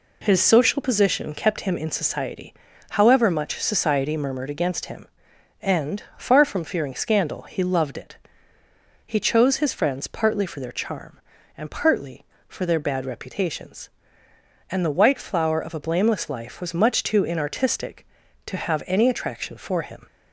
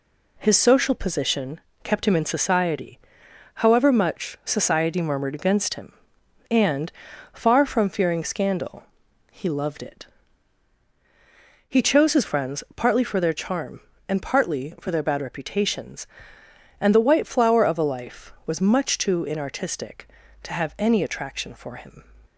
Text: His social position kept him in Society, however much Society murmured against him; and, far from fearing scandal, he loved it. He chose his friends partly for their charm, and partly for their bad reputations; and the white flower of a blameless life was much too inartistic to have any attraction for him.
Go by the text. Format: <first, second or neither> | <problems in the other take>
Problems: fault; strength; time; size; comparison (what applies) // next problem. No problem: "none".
first | pauses between "position" and "kept"; slight; at 1.5 s; 0.24 s long // skips "blameless"; at 17.8 s